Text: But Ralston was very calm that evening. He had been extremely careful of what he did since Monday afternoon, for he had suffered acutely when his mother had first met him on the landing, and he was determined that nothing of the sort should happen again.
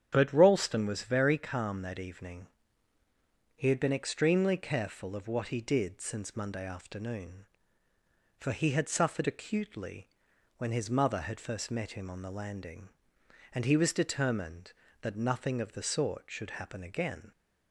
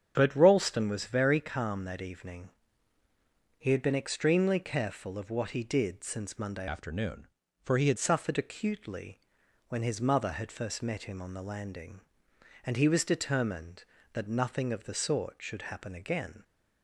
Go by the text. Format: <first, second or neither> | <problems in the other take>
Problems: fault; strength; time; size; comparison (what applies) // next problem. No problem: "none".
first | starts louder than the rest; strong; until 1.1 s; 8 dB; strong in the first // changes voice from "afternoon" to "had"; from 6.6 to 7.9 s; 1.3 s long // pauses between "acutely" and "when"; noticeable; at 9.1 s; 0.50 s long; noticeable in the first